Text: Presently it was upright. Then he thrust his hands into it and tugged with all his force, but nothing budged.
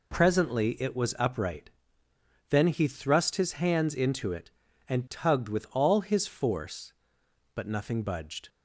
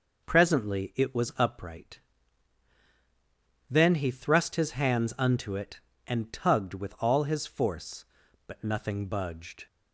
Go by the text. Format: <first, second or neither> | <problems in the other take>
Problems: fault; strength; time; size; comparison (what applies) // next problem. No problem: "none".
first | says "unto" for "into"; at 5.1 s